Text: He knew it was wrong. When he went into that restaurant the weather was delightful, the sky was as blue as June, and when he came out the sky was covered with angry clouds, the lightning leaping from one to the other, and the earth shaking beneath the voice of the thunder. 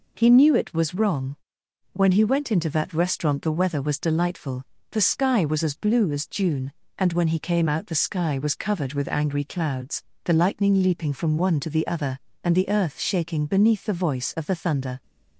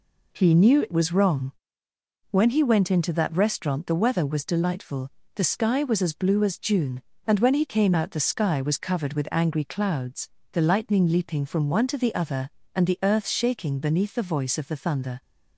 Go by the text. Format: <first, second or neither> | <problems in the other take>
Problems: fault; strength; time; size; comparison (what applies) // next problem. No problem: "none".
neither | none